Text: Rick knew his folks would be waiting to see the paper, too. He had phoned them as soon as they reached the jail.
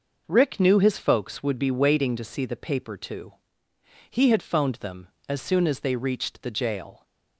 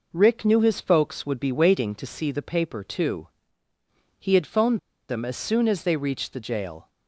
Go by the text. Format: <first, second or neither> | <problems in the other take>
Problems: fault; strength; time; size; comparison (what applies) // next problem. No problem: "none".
first | pauses between "phoned" and "them"; slight; at 4.7 s; 0.29 s long